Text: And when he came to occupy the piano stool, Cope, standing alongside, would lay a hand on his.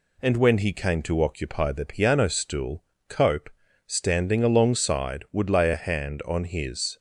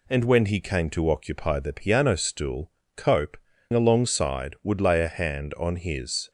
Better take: first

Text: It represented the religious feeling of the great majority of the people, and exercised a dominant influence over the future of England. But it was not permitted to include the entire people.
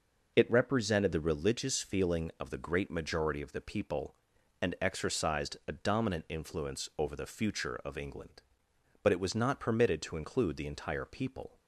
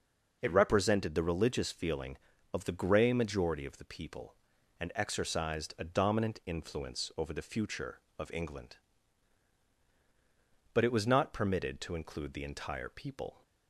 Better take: first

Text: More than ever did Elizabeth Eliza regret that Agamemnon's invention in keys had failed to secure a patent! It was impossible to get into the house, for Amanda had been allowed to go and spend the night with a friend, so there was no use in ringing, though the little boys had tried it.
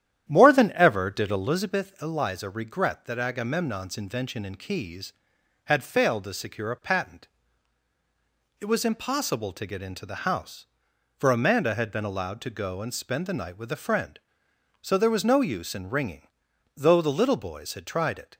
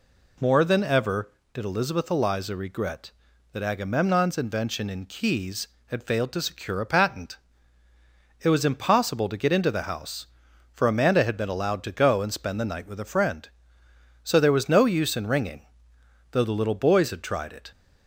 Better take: second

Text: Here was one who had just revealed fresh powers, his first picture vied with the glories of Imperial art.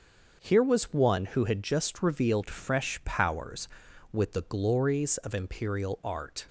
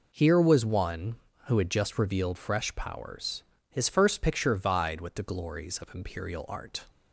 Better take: second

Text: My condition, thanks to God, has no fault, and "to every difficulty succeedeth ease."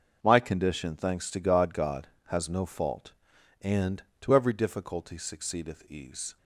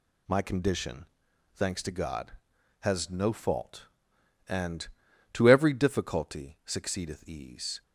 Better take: second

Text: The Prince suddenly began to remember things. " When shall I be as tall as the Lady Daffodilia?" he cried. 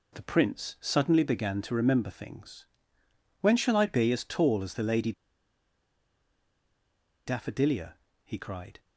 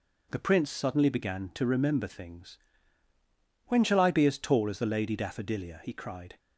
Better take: second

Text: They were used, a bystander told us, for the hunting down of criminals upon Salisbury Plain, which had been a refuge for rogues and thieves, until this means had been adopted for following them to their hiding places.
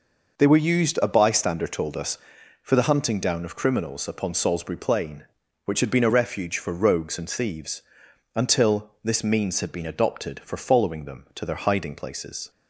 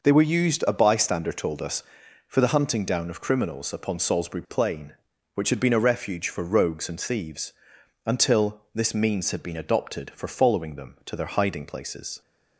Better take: neither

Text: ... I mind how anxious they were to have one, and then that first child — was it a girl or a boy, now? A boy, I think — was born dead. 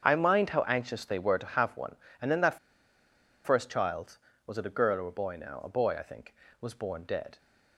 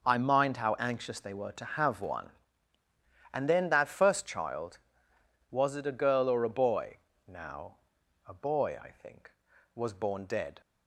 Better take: second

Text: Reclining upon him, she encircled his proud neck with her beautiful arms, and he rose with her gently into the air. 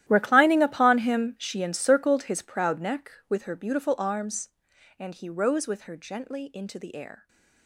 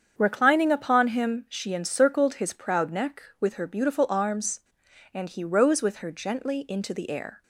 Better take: second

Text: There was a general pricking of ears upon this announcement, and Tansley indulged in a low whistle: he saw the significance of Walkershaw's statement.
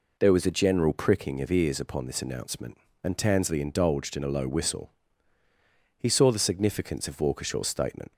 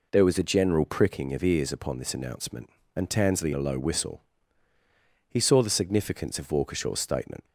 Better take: first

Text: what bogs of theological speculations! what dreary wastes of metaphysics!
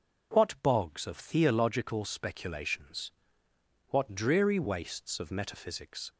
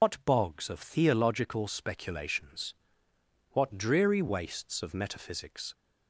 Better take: first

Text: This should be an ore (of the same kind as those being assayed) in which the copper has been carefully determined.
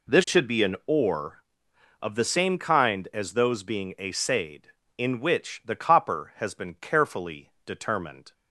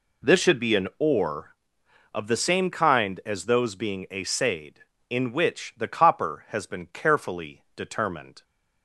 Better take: neither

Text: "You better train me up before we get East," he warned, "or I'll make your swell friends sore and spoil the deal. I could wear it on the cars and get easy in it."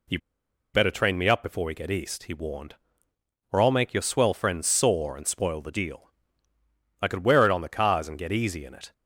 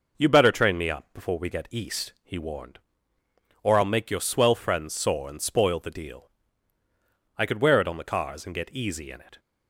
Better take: second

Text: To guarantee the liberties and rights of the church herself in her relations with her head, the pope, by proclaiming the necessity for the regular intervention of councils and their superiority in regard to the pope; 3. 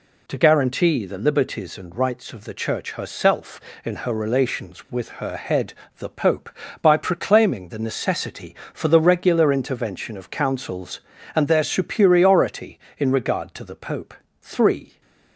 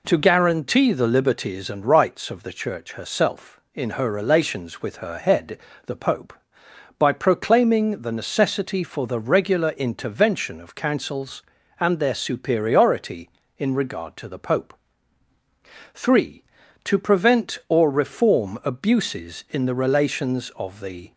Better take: first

